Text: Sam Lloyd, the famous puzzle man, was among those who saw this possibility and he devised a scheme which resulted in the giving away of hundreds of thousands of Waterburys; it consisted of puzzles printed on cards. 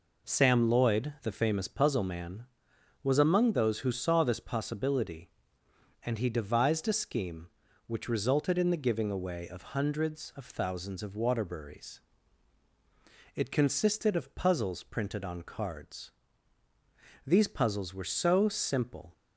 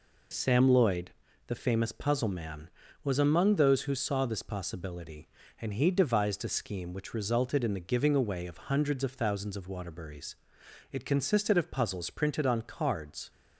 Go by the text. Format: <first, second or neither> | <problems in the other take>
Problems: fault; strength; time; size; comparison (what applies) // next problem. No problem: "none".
second | goes on to say "These puzzles were so simple"; strong; from 17.2 s on; 1.8 s long